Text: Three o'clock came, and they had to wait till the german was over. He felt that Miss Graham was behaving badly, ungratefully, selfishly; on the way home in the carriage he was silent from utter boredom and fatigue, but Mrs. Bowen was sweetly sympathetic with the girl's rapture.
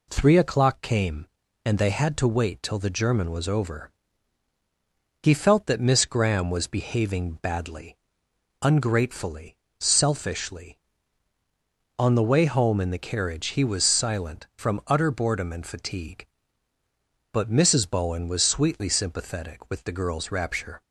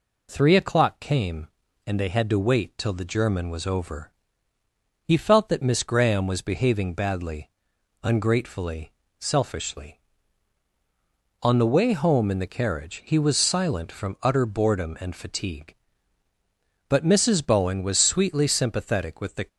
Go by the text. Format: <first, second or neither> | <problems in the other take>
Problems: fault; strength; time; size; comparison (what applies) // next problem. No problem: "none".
first | stops before "girl's rapture"; at 19.4 s